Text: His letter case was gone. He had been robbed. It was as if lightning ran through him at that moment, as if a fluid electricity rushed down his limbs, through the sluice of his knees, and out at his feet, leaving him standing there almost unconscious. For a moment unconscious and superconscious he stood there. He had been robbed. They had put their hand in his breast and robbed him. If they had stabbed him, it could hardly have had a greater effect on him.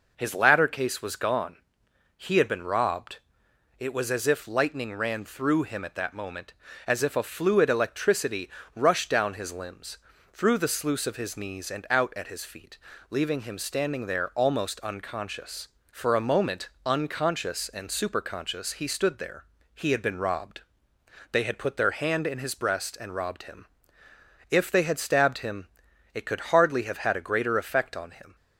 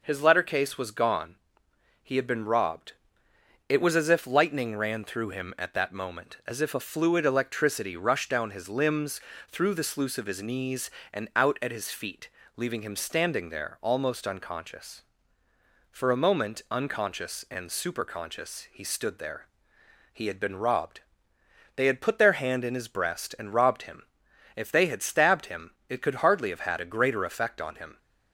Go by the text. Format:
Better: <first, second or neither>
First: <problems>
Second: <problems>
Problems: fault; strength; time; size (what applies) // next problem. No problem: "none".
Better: second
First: says "ladder" for "letter"; at 0.3 s // pauses between "electricity" and "rushed"; slight; at 8.4 s; 0.26 s long // pauses between "moment" and "unconscious"; slight; at 16.6 s; 0.16 s long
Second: none